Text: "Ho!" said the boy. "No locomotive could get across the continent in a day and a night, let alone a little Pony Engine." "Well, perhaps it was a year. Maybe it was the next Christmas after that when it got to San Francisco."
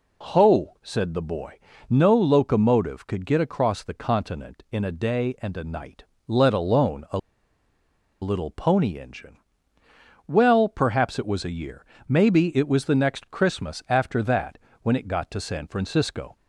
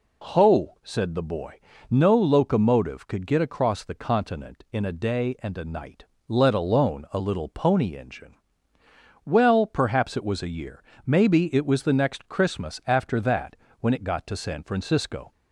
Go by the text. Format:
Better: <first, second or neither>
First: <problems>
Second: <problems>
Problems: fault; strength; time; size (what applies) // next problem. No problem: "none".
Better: second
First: pauses between "a" and "little"; at 7.1 s; 1.0 s long // pauses between "that" and "when"; slight; at 14.5 s; 0.24 s long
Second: pauses between "that" and "when"; slight; at 13.5 s; 0.24 s long